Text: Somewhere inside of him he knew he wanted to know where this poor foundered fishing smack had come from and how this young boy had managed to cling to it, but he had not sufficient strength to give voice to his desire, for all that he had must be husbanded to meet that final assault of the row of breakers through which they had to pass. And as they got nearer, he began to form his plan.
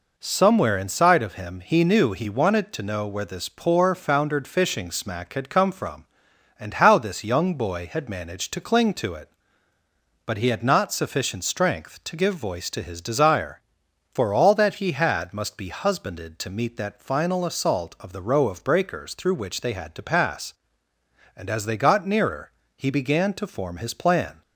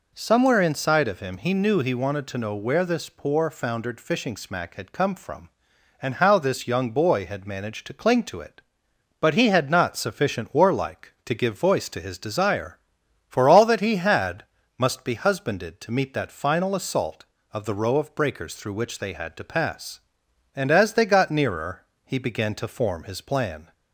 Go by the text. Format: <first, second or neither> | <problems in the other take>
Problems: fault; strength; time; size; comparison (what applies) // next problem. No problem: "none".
first | says "warlike" for "strength"; at 10.5 s // pauses between "had" and "must"; slight; at 14.4 s; 0.32 s long